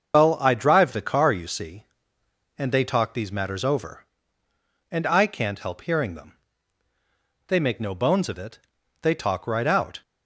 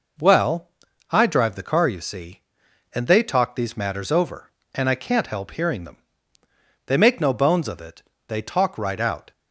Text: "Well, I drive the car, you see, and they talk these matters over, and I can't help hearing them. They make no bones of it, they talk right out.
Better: second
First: loses the start of "Well"; at 0.1 s; 70 ms // starts louder than the rest; until 1.1 s; 6.5 dB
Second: none

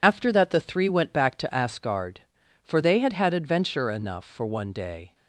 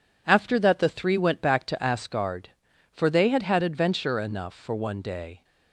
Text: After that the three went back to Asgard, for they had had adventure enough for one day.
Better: second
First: loses the start of "After"; at 0.0 s; 35 ms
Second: none

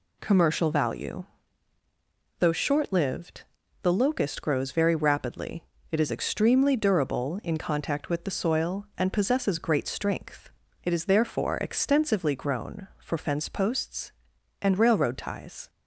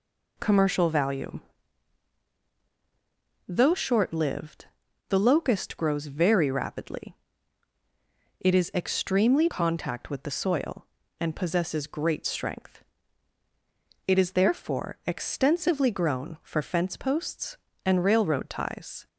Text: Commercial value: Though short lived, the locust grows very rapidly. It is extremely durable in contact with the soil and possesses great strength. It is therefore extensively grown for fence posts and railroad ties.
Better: first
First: none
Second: skips "durable in"; at 9.4 s

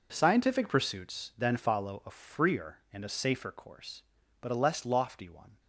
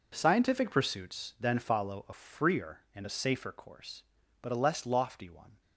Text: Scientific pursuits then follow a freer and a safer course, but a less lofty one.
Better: neither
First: none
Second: none

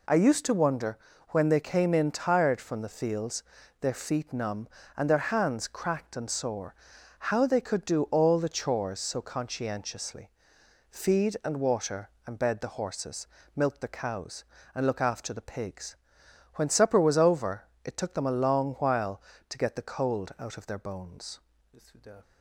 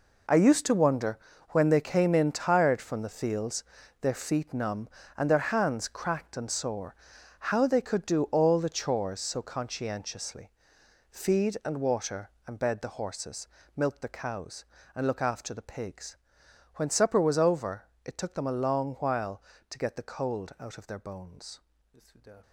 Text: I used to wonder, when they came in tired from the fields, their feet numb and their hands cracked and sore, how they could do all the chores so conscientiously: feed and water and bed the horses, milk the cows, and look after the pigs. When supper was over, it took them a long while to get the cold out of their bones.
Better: first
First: none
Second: gets quieter; strong; throughout; 11 dB

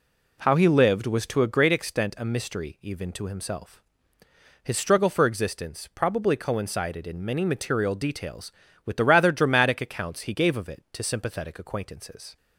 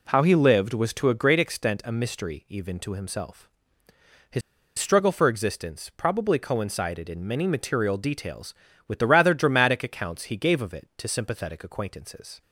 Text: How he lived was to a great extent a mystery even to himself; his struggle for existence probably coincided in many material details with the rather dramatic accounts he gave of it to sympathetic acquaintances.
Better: first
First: none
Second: pauses between "his" and "struggle"; at 4.4 s; 0.38 s long

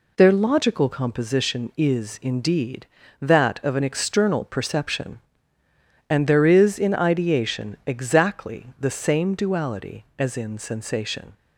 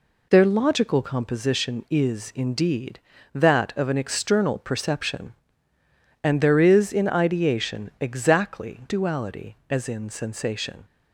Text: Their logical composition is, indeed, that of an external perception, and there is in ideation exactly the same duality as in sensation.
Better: first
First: none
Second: skips "the same"; at 8.8 s

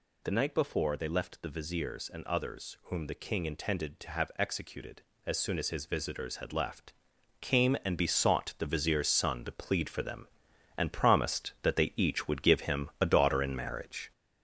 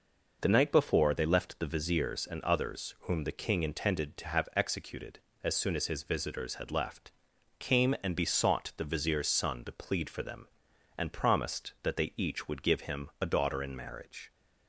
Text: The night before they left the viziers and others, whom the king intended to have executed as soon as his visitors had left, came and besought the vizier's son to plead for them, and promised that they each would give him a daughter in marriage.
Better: second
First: gets louder; noticeable; throughout; 5 dB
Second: none

